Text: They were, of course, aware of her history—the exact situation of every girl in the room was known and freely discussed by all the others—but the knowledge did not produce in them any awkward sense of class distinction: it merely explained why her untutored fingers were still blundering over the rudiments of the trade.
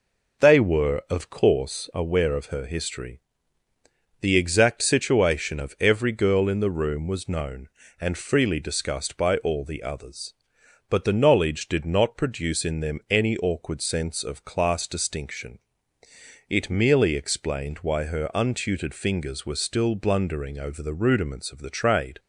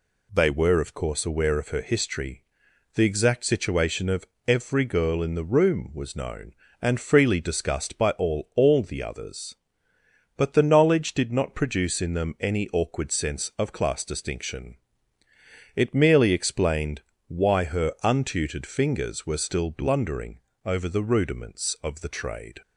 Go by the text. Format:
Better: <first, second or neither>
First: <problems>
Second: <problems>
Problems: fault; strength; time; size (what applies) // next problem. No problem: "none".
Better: first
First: none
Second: pauses between "of" and "every"; slight; at 4.2 s; 0.22 s long // says "all" twice; at 8.5 s // pauses between "explained" and "why"; slight; at 17.0 s; 0.26 s long // pauses between "blundering" and "over"; slight; at 20.4 s; 0.22 s long